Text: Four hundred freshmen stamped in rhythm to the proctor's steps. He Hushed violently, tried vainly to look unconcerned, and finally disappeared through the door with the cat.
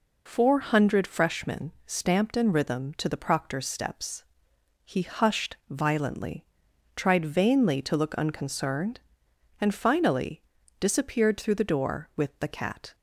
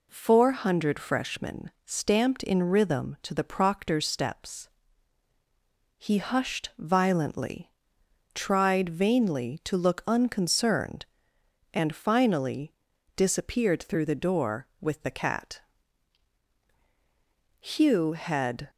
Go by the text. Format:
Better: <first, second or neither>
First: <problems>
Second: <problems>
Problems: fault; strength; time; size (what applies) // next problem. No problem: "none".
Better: first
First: pauses between "freshmen" and "stamped"; slight; at 1.7 s; 0.16 s long // pauses between "finally" and "disappeared"; at 10.4 s; 0.38 s long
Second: pauses between "freshmen" and "stamped"; slight; at 1.6 s; 0.16 s long // pauses between "finally" and "disappeared"; at 12.7 s; 0.44 s long // goes on to say "Hugh had"; noticeable; from 17.5 s on; 1.1 s long